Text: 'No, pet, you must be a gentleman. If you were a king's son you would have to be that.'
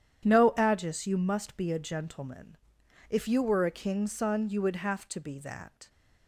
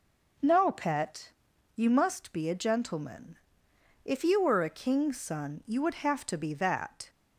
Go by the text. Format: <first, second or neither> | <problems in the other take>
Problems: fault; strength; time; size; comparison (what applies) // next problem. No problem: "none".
second | starts louder than the rest; strong; until 1.2 s; 9.5 dB // says "agis" for "pet"; at 0.5 s